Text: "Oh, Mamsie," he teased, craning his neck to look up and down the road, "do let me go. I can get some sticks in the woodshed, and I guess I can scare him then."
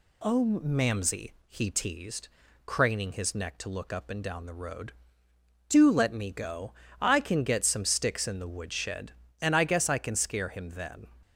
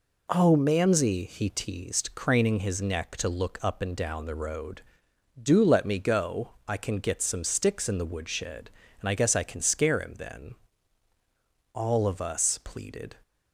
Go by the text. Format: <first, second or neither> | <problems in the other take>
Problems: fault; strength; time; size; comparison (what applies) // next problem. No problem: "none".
first | goes on to say "All of us pleaded"; from 11.7 s on; 1.4 s long